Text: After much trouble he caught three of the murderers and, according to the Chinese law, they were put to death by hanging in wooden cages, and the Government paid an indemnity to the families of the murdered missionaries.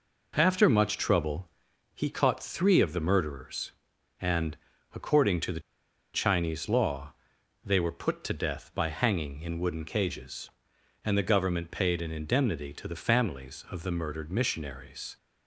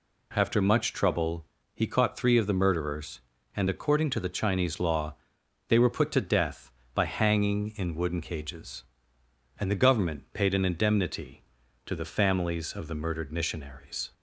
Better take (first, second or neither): second